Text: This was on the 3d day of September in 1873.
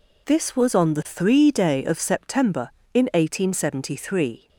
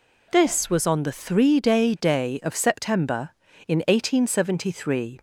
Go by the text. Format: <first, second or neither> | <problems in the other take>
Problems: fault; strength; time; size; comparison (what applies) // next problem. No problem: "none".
first | says "day" twice; at 1.9 s